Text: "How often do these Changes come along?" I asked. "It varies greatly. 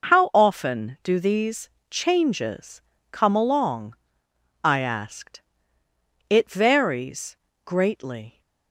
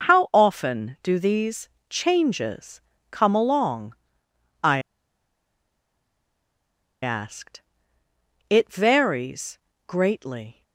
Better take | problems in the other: first | pauses between "these" and "Changes"; slight; at 1.6 s; 0.20 s long; slight in the first // pauses between "Changes" and "come"; slight; at 2.7 s; 0.32 s long; slight in the first // pauses between "I" and "asked"; strong; at 4.7 s; 2.2 s long // pauses between "varies" and "greatly"; slight; at 9.5 s; 0.30 s long; slight in the first

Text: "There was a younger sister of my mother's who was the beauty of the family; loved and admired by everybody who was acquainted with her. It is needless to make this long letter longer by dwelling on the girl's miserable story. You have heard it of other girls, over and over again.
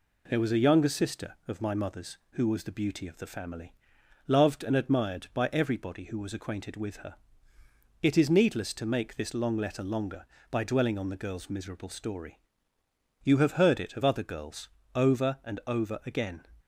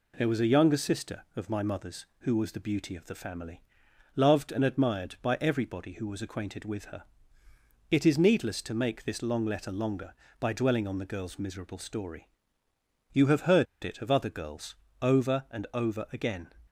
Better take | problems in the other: first | pauses between "heard" and "it"; slight; at 13.6 s; 0.18 s long

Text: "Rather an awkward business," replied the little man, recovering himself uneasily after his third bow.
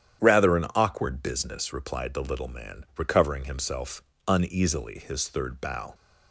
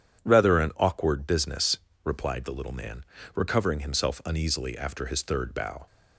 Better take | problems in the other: second | starts louder than the rest; strong; until 1.2 s; 9.5 dB // pauses between "himself" and "uneasily"; slight; at 4.0 s; 0.26 s long // skips "after"; at 4.9 s

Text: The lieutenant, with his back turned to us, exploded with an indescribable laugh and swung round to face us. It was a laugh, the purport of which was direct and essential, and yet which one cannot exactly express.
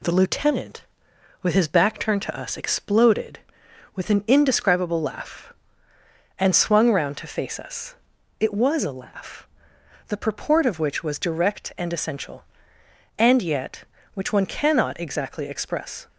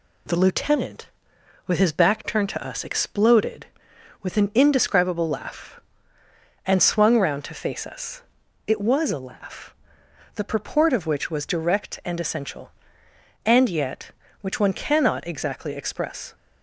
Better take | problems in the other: neither | none

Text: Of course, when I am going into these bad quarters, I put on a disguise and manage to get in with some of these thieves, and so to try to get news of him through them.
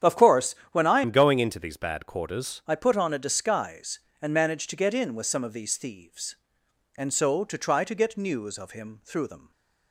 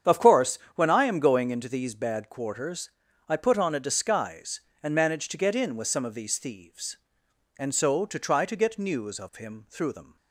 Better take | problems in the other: second | starts louder than the rest; strong; until 1.2 s; 9 dB; strong in the second // changes voice from "am" to "quarters"; from 1.0 to 2.6 s; 1.6 s long // stays silent after the last word; slight; from 9.3 s on; 0.6 s long

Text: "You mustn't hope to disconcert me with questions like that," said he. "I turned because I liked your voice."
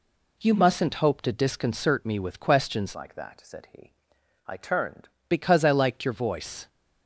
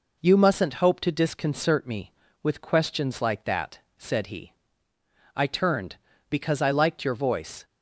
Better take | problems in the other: second | changes voice from "like" to "turned"; from 2.9 to 5.0 s; 2.1 s long

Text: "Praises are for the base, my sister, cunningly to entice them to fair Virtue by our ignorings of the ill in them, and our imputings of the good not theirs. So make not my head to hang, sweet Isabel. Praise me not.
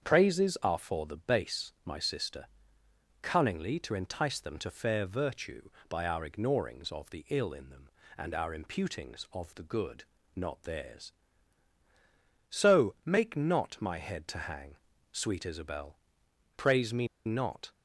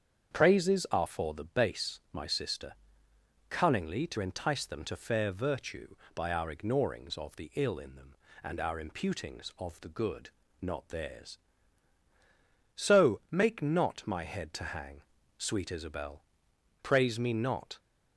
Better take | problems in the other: second | starts louder than the rest; strong; until 1.0 s; 7.5 dB; strong in the second // pauses between "good" and "not"; slight; at 10.0 s; 0.32 s long; slight in the second // pauses between "me" and "not"; slight; at 17.0 s; 0.18 s long

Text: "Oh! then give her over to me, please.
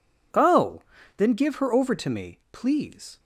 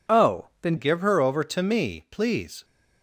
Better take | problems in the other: first | changes voice at "give"; from 0.7 s on; 1.9 s long

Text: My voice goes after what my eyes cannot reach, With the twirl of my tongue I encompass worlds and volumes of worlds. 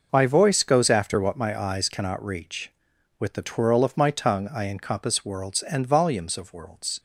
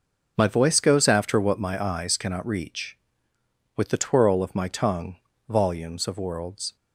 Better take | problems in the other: first | skips "I encompass worlds and"; at 5.3 s

